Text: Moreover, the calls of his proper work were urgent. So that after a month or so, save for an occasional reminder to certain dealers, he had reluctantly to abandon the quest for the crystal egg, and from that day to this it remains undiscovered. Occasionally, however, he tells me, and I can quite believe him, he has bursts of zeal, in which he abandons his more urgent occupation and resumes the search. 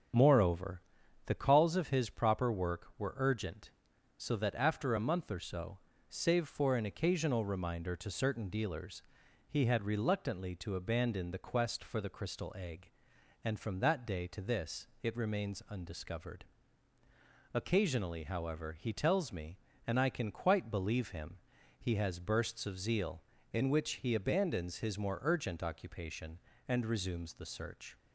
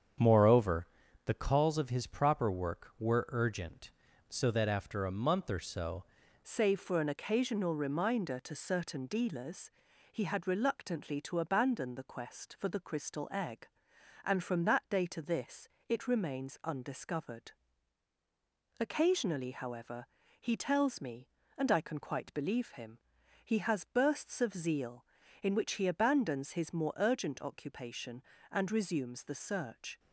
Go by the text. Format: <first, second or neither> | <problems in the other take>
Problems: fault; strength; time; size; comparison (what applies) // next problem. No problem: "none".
first | starts louder than the rest; strong; until 1.5 s; 8 dB; strong in the first // changes voice at "save"; from 6.4 s on; 23.5 s long // pauses between "this" and "it"; slight; at 15.6 s; 0.22 s long; slight in the first